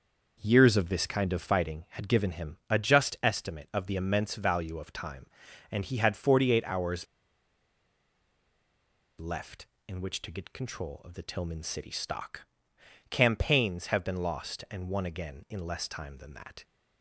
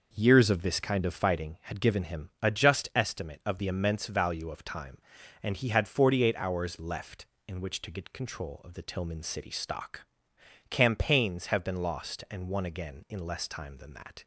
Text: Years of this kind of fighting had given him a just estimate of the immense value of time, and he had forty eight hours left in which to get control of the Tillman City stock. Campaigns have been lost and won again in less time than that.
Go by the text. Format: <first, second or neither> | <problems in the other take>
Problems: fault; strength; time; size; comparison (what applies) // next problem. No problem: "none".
second | pauses between "hours" and "left"; strong; at 7.0 s; 2.1 s long